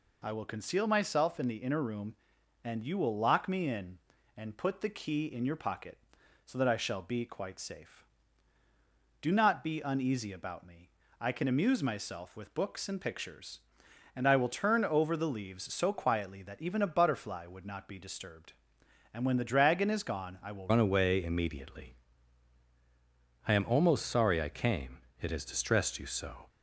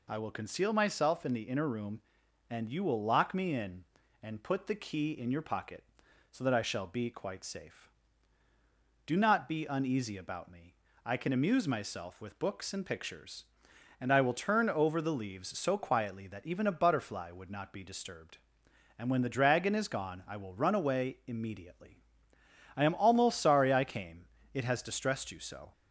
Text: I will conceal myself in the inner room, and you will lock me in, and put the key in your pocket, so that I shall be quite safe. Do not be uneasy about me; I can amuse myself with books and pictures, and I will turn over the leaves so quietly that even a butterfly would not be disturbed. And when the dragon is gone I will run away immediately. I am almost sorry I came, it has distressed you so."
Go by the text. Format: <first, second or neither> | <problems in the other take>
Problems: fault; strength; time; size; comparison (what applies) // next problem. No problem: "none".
second | changes voice at "run"; from 20.7 s on; 5.7 s long